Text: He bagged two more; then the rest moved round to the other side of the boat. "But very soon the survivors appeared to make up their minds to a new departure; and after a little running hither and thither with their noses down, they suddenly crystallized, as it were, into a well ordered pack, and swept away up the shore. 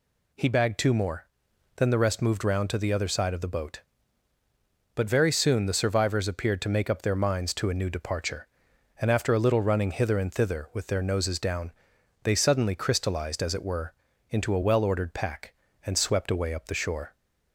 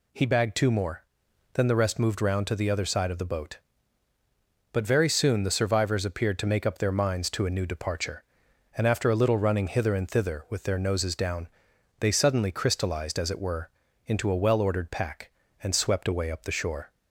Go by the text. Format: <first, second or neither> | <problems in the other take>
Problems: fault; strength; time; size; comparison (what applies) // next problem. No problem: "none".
neither | none